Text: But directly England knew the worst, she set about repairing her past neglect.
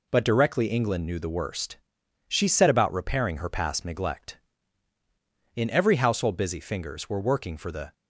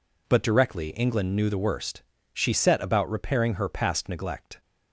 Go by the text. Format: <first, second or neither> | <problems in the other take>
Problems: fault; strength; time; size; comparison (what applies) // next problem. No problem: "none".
second | goes on to say "In every household busy fingers were working for the"; strong; from 5.5 s on; 2.3 s long